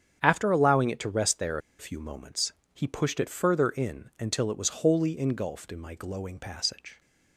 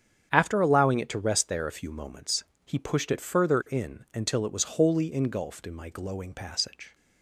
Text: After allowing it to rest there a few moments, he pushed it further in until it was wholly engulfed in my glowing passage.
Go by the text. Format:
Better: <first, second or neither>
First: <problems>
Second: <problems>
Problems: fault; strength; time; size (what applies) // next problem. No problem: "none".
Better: second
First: starts louder than the rest; strong; until 1.2 s; 8.5 dB // pauses between "there" and "a"; slight; at 1.5 s; 0.21 s long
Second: starts louder than the rest; strong; until 1.3 s; 8.5 dB